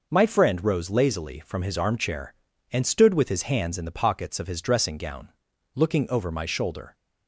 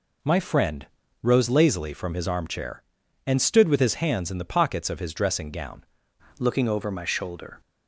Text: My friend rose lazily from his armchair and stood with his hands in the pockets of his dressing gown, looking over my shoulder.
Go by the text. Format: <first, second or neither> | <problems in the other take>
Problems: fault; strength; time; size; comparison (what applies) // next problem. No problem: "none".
first | pauses between "friend" and "rose"; slight; at 0.8 s; 0.36 s long // changes voice at "looking"; from 6.3 s on; 1.3 s long